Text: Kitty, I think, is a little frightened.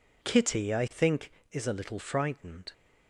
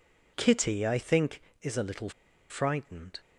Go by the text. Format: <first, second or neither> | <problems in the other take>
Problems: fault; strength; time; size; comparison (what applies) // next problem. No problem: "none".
first | pauses between "little" and "frightened"; at 2.0 s; 0.40 s long